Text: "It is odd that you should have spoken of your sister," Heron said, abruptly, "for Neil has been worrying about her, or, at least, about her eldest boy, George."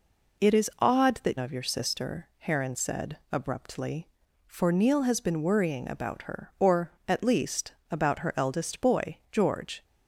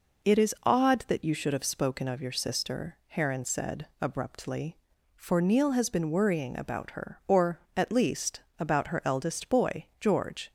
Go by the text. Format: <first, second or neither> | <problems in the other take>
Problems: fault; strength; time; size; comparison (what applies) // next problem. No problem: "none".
second | skips "you should have spoken"; at 1.3 s